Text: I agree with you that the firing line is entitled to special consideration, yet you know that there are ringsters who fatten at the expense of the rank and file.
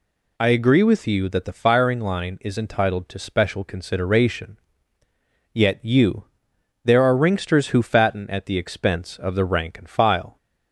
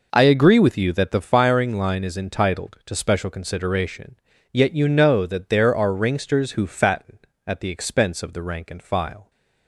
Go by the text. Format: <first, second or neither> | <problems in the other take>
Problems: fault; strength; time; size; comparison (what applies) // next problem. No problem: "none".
second | skips "know that"; at 6.5 s